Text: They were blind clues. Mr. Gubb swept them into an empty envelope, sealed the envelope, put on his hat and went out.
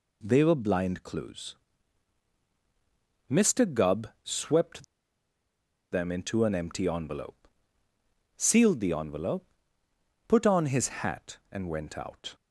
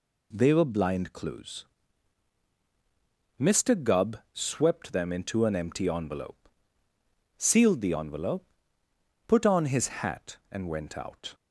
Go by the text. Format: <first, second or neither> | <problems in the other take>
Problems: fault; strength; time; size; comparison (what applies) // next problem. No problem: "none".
second | pauses between "Gubb" and "swept"; slight; at 4.0 s; 0.16 s long; slight in the second // pauses between "swept" and "them"; at 4.8 s; 1.0 s long // pauses between "his" and "hat"; slight; at 10.8 s; 0.16 s long; slight in the second